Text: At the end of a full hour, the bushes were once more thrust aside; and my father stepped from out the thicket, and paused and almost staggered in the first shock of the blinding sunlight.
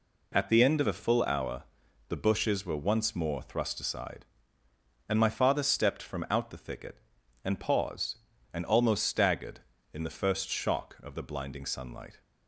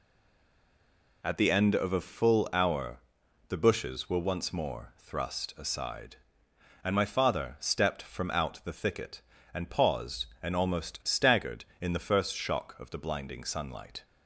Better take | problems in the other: first | stays silent before the first word; noticeable; until 1.2 s; 1.2 s long

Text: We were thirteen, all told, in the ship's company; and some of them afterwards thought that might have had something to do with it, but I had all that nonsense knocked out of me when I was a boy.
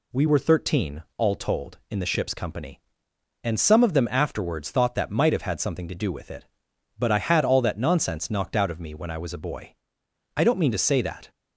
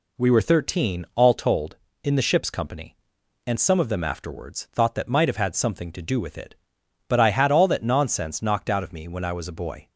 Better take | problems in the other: second | goes on to say "I don't mean to say that"; noticeable; from 10.3 s on; 0.94 s long

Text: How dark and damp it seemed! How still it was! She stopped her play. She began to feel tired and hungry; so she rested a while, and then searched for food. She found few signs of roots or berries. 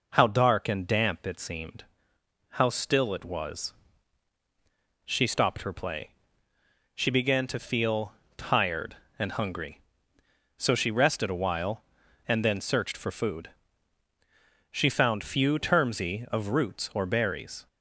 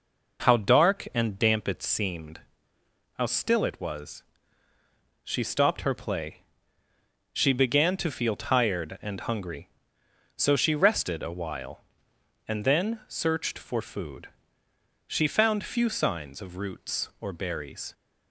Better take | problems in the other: second | pauses between "feel" and "tired"; slight; at 8.1 s; 0.22 s long // says "termsy" for "signs"; at 15.5 s

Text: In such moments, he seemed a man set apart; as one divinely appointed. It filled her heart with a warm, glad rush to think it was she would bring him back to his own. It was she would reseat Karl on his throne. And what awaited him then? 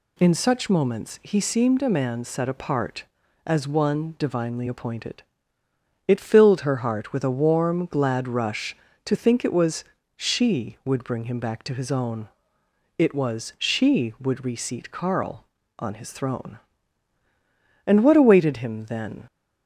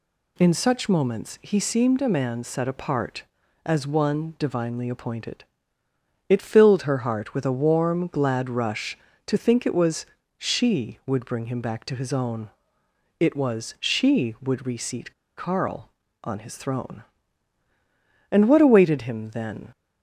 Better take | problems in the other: first | pauses between "was" and "she"; slight; at 10.0 s; 0.32 s long; slight in the first // pauses between "reseat" and "Karl"; slight; at 15.1 s; 0.23 s long

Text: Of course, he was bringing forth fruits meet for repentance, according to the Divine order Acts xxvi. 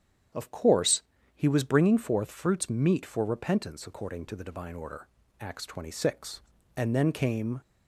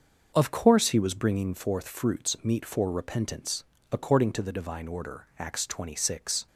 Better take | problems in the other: second | starts louder than the rest; strong; until 1.6 s; 9 dB; also in the second // pauses between "order" and "Acts"; slight; at 5.0 s; 0.32 s long // goes on to say "And then came"; noticeable; from 6.7 s on; 0.86 s long

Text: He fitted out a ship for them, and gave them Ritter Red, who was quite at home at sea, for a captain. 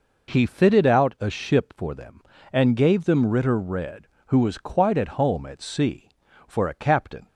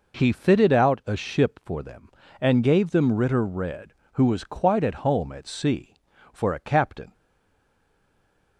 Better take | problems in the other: first | stays silent after the last word; noticeable; from 7.1 s on; 1.4 s long

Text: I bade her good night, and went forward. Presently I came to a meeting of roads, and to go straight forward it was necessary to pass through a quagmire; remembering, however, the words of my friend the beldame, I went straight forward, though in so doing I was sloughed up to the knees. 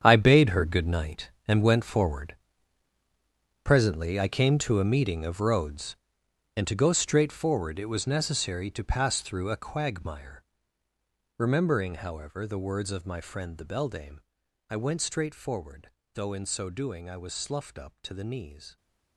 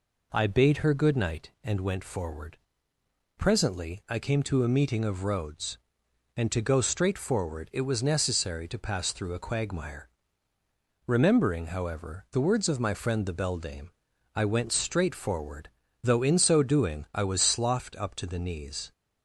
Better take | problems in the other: second | gets quieter; strong; throughout; 13 dB

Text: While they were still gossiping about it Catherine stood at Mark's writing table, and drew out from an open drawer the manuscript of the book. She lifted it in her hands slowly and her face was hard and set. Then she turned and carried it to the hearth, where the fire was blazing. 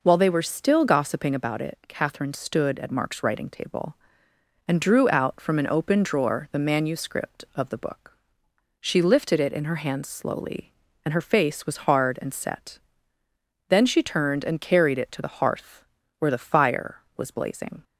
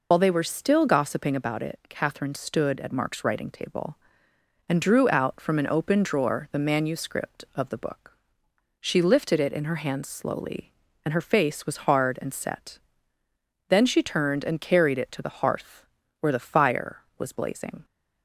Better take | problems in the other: first | loses the start of "While"; at 0.1 s; 70 ms

